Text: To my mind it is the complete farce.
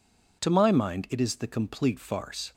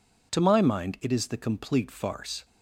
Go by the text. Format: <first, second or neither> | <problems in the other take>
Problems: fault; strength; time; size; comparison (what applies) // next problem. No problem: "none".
neither | none